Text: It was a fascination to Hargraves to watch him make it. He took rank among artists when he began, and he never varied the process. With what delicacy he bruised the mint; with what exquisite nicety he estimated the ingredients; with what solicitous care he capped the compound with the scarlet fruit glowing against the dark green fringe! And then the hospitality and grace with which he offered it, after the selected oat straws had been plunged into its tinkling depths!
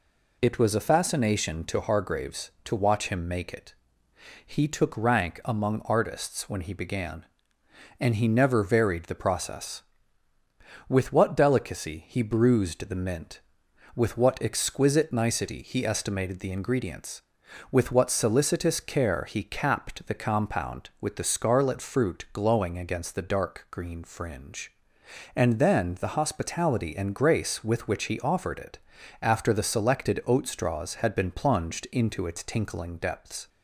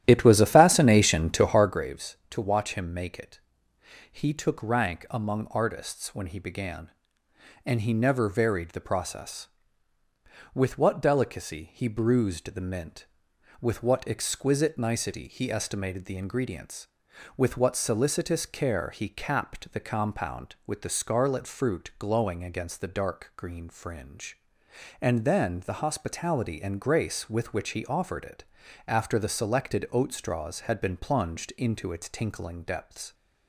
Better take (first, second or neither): first